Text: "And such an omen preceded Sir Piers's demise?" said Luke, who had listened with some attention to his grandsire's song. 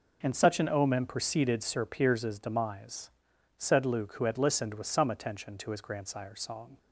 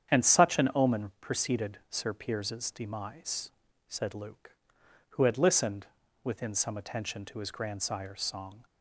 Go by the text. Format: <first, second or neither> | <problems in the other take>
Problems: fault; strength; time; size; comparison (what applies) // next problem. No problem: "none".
first | starts louder than the rest; strong; until 1.2 s; 8.5 dB // says "within" for "with"; at 6.2 s